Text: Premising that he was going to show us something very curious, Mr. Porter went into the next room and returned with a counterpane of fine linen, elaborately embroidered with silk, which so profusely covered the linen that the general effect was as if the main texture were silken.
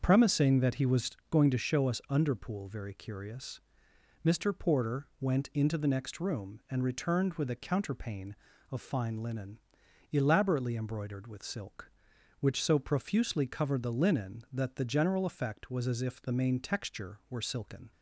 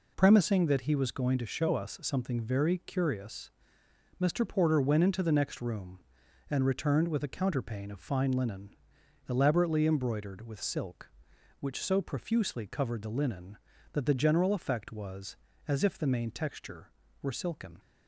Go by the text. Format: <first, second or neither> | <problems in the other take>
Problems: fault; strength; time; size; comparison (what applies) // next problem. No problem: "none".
second | starts louder than the rest; until 1.0 s; 6.5 dB // pauses between "was" and "going"; slight; at 1.1 s; 0.18 s long // says "underpool" for "something"; at 2.0 s